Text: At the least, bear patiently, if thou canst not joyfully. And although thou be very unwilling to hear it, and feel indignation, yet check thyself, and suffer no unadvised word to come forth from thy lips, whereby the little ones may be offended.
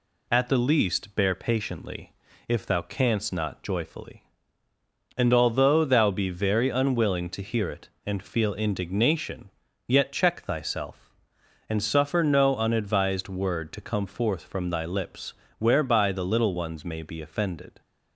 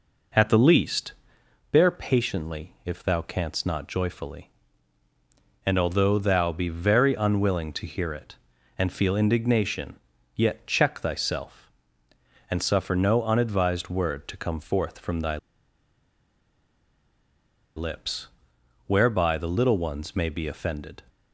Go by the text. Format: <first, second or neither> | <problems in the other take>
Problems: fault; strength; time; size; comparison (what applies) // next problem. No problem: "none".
first | pauses between "thy" and "lips"; strong; at 15.3 s; 2.3 s long